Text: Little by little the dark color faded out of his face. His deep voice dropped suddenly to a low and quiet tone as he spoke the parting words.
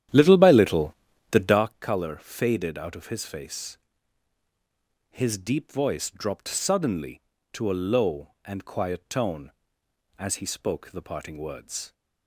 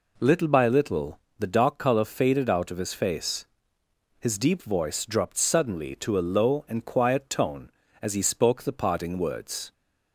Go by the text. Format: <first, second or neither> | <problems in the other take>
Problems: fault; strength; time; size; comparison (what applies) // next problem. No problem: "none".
second | starts louder than the rest; strong; until 1.7 s; 10.5 dB // pauses between "little" and "the"; slight; at 0.9 s; 0.36 s long; slight in the second